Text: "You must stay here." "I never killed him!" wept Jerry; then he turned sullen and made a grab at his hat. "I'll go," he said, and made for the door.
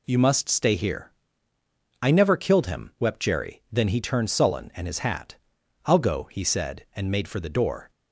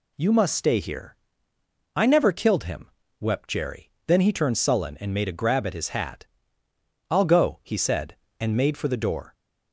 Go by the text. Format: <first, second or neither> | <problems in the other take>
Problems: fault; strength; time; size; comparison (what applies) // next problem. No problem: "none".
second | skips "made a grab at"; at 4.8 s